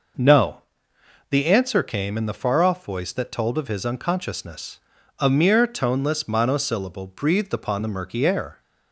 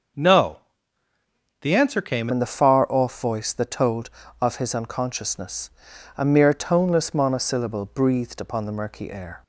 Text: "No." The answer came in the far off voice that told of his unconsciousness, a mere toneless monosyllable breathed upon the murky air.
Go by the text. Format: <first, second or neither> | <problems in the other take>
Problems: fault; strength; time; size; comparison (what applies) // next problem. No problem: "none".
first | starts louder than the rest; until 2.1 s; 6.5 dB // changes voice at "in"; from 2.3 s on; 7.1 s long